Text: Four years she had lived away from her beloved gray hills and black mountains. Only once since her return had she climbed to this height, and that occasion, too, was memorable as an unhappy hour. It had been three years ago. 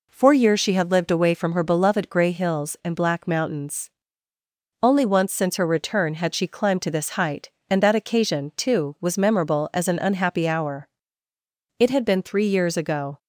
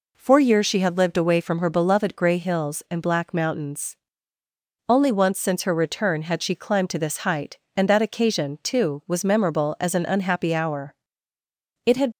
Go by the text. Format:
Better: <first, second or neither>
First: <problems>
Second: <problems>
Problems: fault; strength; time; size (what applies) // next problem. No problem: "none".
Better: first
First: none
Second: stops before "been three years ago"; at 12.1 s